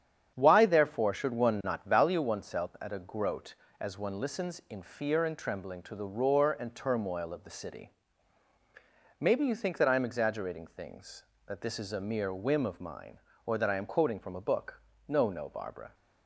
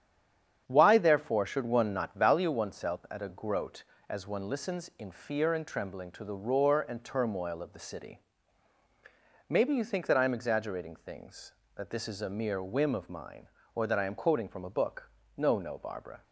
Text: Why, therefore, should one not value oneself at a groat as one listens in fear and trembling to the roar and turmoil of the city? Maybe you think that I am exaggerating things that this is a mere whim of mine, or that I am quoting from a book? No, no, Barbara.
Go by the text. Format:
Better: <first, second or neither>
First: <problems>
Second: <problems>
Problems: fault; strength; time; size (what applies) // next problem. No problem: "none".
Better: first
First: starts louder than the rest; strong; until 1.3 s; 8.5 dB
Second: stays silent before the first word; slight; until 0.6 s; 0.6 s long // starts louder than the rest; strong; until 1.6 s; 8.5 dB